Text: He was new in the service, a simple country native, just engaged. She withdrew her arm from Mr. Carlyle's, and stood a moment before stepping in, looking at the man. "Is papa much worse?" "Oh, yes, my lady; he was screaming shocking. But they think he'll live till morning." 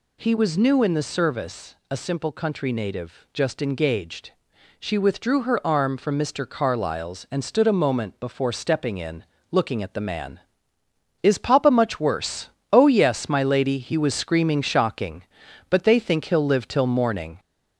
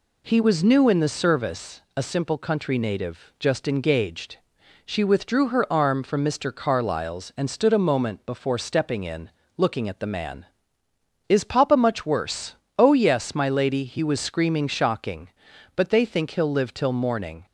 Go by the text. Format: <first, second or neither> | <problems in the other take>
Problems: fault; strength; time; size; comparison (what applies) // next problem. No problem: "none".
second | gets louder; slight; throughout; 3 dB